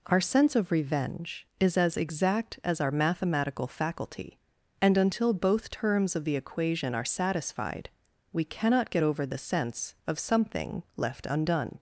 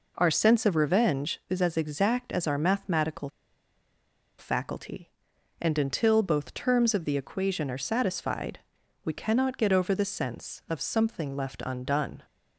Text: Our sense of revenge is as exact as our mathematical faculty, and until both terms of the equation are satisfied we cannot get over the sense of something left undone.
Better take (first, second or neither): first